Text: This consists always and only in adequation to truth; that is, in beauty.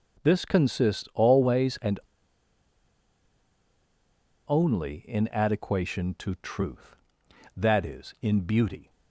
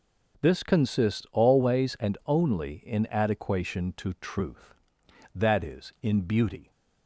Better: second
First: pauses between "and" and "only"; strong; at 1.9 s; 2.4 s long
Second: none

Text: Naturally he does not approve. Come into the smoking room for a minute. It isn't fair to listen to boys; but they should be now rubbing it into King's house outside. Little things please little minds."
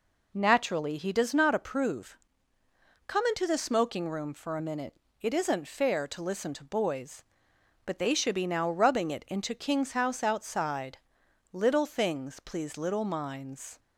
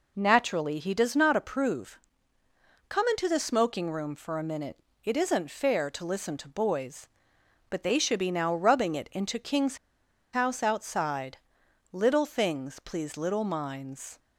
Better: first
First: none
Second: pauses between "King's" and "house"; noticeable; at 9.7 s; 0.55 s long

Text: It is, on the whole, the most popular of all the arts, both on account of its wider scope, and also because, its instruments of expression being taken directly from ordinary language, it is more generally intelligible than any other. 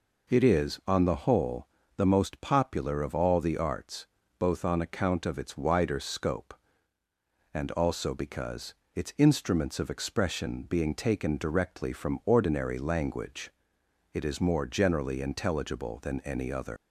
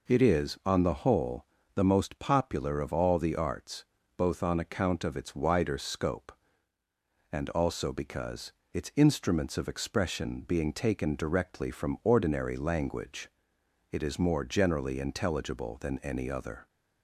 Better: second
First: leaves "other" unfinished; at 16.7 s; 130 ms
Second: none

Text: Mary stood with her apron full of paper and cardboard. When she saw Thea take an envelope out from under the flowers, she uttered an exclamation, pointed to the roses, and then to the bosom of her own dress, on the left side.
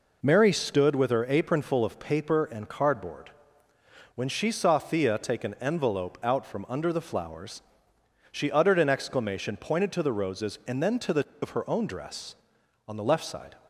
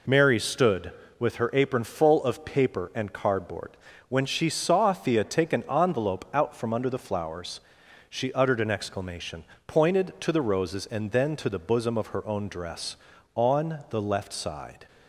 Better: second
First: skips "bosom"; at 11.3 s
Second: none

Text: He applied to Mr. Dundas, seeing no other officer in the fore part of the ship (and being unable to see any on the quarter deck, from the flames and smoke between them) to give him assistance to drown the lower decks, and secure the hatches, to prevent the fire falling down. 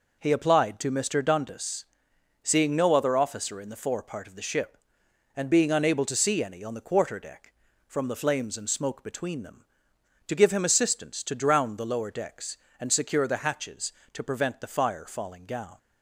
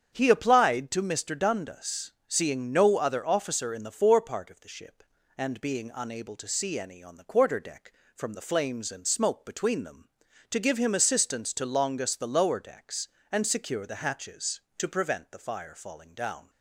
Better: first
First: none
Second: starts louder than the rest; strong; until 1.1 s; 7.5 dB // says "longus" for "drown"; at 11.6 s

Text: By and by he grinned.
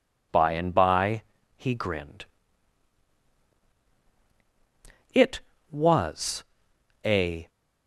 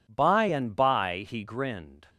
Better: second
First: pauses between "by" and "he"; slight; at 1.2 s; 0.32 s long // goes on to say "It was a"; strong; from 5.1 s on; 2.3 s long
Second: none

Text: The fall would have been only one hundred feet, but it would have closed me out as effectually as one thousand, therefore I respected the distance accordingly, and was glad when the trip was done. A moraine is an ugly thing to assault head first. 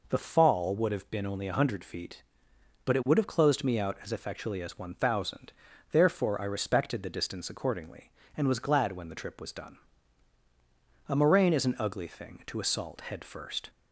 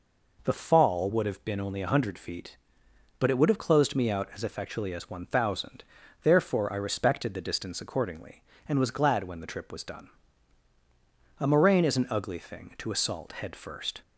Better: neither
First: none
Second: none

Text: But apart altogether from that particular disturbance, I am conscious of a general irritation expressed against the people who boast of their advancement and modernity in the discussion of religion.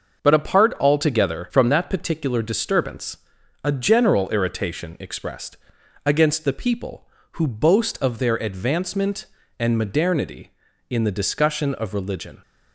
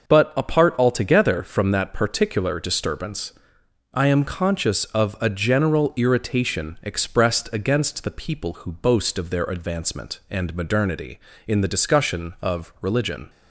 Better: second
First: starts louder than the rest; until 1.2 s; 6.5 dB // skips "I am conscious of"; at 3.4 s // pauses between "expressed" and "against"; noticeable; at 5.5 s; 0.50 s long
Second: starts louder than the rest; until 1.1 s; 6 dB

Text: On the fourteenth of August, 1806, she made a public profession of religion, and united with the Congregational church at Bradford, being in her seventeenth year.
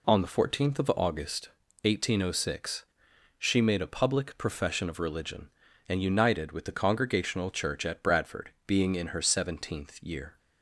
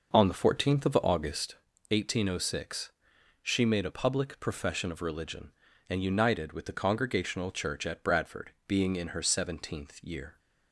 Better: first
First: none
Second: starts louder than the rest; noticeable; until 1.5 s; 5.5 dB

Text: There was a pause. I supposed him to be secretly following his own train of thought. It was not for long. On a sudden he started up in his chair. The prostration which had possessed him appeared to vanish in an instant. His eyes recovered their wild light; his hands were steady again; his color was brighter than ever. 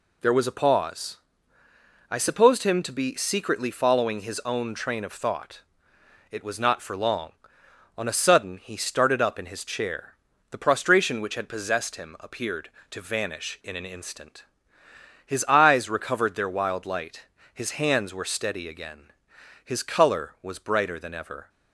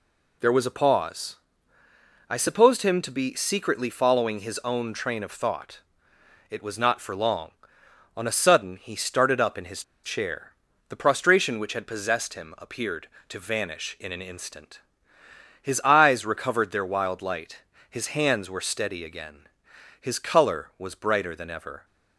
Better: first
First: none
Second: pauses between "his" and "chair"; slight; at 9.8 s; 0.22 s long

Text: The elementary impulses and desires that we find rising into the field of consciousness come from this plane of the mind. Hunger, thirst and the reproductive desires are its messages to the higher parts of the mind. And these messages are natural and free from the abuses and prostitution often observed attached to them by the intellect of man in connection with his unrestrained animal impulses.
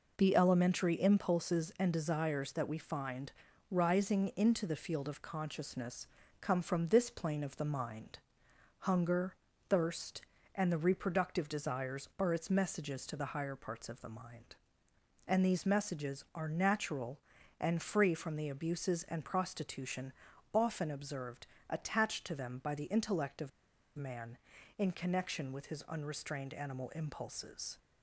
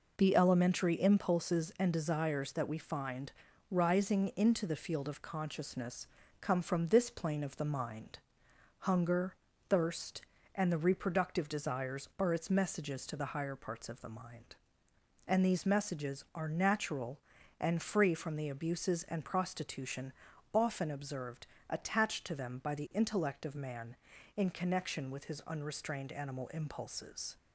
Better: second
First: pauses between "find" and "rising"; at 3.3 s; 0.38 s long // pauses between "consciousness" and "come"; slight; at 6.0 s; 0.34 s long // pauses between "prostitution" and "often"; at 20.1 s; 0.40 s long // pauses between "observed" and "attached"; slight; at 21.4 s; 0.20 s long // pauses between "of" and "man"; at 23.4 s; 0.45 s long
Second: pauses between "find" and "rising"; at 3.3 s; 0.38 s long // pauses between "consciousness" and "come"; slight; at 6.0 s; 0.34 s long // pauses between "prostitution" and "often"; at 20.1 s; 0.40 s long // pauses between "observed" and "attached"; slight; at 21.4 s; 0.20 s long

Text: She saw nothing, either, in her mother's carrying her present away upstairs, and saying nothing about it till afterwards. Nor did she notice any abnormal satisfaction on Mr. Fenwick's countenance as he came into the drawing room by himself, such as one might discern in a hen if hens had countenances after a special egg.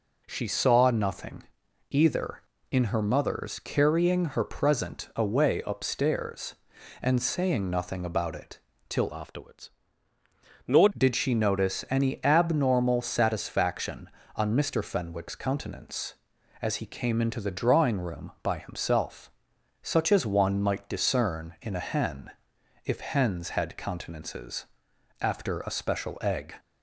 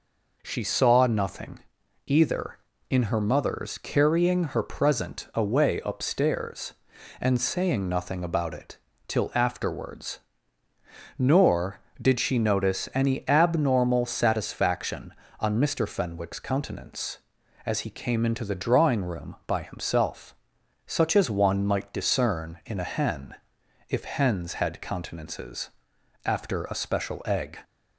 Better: second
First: pauses between "it" and "till"; slight; at 8.5 s; 0.30 s long // changes voice from "afterwards" to "Nor"; from 9.1 to 10.8 s; 1.7 s long // pauses between "hen" and "if"; noticeable; at 22.2 s; 0.56 s long // pauses between "countenances" and "after"; noticeable; at 24.6 s; 0.54 s long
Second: pauses between "it" and "till"; slight; at 8.7 s; 0.30 s long // pauses between "hen" and "if"; noticeable; at 23.3 s; 0.56 s long // pauses between "countenances" and "after"; noticeable; at 25.7 s; 0.54 s long

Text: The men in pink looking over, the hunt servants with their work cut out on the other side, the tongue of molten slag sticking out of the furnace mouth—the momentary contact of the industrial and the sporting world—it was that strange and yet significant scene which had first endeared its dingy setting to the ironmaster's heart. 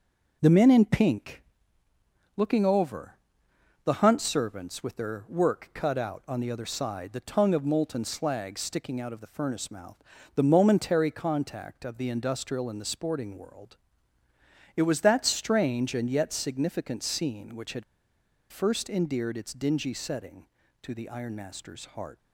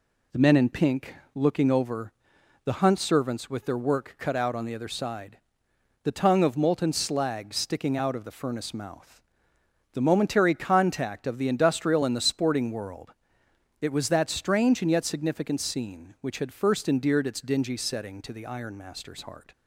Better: second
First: pauses between "pink" and "looking"; noticeable; at 1.4 s; 0.96 s long // pauses between "had" and "first"; noticeable; at 17.8 s; 0.67 s long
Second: pauses between "pink" and "looking"; slight; at 1.1 s; 0.20 s long

